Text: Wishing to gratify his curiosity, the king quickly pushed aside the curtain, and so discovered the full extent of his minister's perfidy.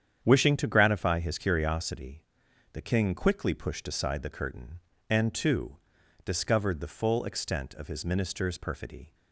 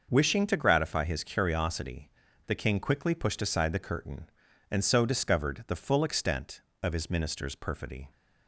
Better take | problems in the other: second | starts louder than the rest; strong; until 1.2 s; 8.5 dB // says "too" for "so"; at 5.3 s

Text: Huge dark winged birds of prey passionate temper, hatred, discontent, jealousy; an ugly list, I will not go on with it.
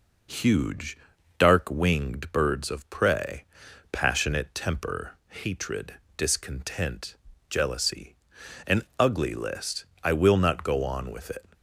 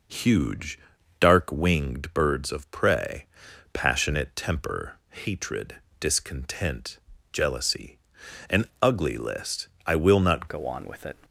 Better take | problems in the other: first | pauses between "Huge" and "dark"; at 0.7 s; 0.44 s long; also in the first // pauses between "prey" and "passionate"; noticeable; at 3.2 s; 0.46 s long; noticeable in the first // pauses between "an" and "ugly"; slight; at 8.6 s; 0.18 s long; slight in the first // changes voice at "go"; from 10.4 s on; 0.7 s long

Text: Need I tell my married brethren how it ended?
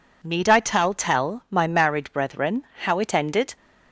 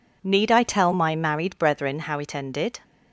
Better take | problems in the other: second | says "tell" twice; at 0.9 s // pauses between "brethren" and "how"; slight; at 2.6 s; 0.20 s long

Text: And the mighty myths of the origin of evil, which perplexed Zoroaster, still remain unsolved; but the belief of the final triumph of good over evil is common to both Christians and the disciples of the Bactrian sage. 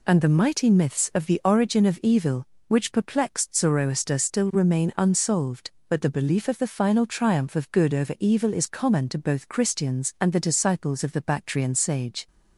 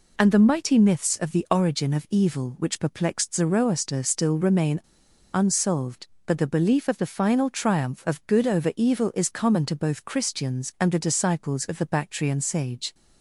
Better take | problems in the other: first | pauses between "remain" and "unsolved"; noticeable; at 4.8 s; 0.54 s long

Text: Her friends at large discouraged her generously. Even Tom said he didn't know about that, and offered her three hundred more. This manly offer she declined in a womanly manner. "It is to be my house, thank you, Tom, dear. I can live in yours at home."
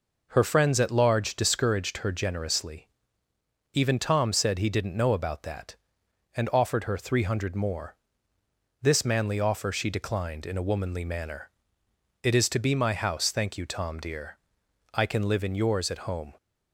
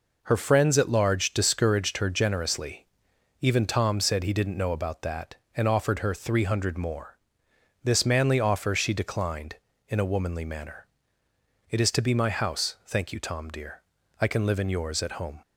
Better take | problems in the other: neither | none

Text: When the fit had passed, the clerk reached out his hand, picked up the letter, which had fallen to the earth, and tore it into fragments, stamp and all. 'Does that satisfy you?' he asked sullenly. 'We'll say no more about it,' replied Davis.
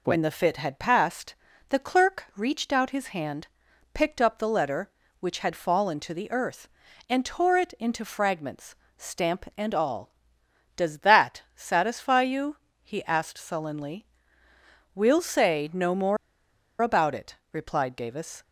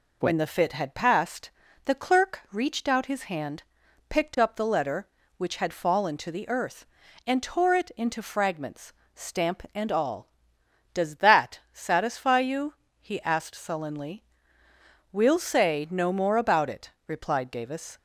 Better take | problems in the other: second | pauses between "more" and "about"; noticeable; at 16.1 s; 0.65 s long

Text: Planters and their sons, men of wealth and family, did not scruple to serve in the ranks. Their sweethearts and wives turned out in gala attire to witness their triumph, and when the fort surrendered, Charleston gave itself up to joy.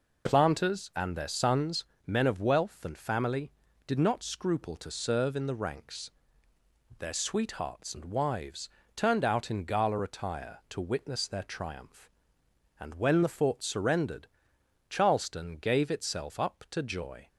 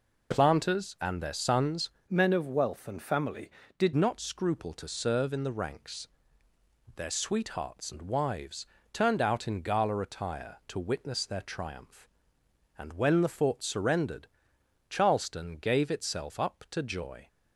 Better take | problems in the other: first | changes voice from "men" to "did"; from 2.1 to 3.9 s; 1.8 s long // pauses between "wives" and "turned"; slight; at 8.6 s; 0.28 s long; slight in the first

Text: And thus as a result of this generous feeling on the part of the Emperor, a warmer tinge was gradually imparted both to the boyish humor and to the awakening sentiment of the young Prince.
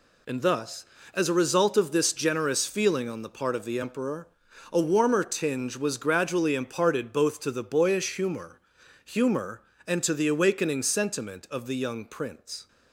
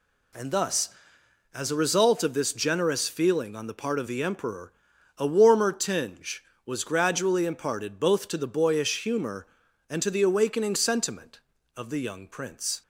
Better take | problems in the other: second | says "humor" twice; at 9.0 s

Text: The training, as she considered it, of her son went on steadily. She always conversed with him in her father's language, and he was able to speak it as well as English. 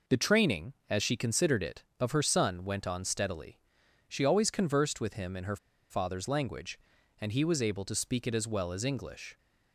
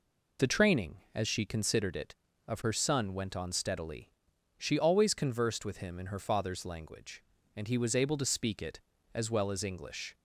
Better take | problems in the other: second | pauses between "her" and "father's"; slight; at 5.5 s; 0.34 s long

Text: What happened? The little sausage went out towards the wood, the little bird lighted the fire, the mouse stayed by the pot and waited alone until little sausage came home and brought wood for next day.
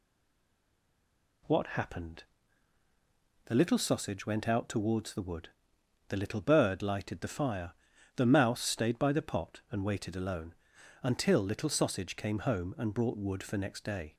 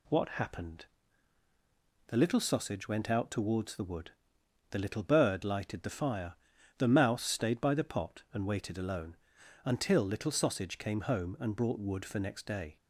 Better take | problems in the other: second | stays silent before the first word; noticeable; until 1.4 s; 1.4 s long // pauses between "alone" and "until"; noticeable; at 10.5 s; 0.48 s long; noticeable in the second

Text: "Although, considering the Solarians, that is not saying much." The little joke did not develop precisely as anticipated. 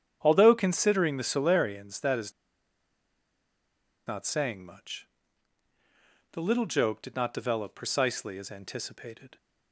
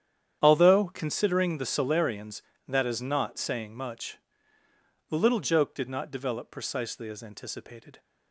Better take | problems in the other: second | starts louder than the rest; strong; until 1.2 s; 8.5 dB; strong in the second // pauses between "is" and "not"; strong; at 2.3 s; 1.7 s long

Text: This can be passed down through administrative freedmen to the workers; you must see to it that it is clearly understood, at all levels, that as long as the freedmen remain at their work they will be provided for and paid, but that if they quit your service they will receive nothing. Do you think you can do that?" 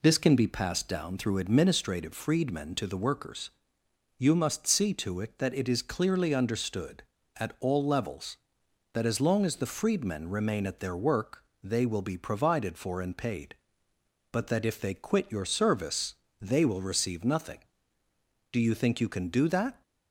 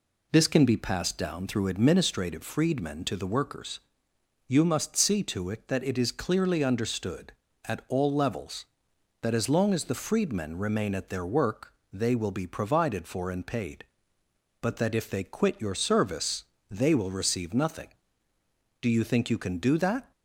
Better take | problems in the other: neither | pauses between "work" and "they"; slight; the same in both // pauses between "service" and "they"; slight; the same in both

